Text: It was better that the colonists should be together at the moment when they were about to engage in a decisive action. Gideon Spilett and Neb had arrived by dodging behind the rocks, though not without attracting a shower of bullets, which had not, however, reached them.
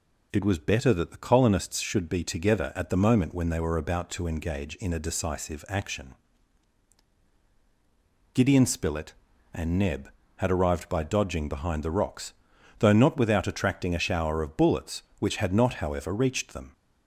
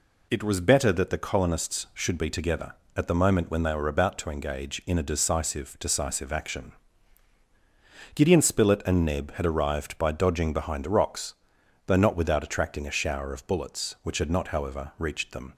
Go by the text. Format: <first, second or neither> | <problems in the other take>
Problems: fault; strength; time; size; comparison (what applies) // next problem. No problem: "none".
first | says "decisive" twice; at 5.7 s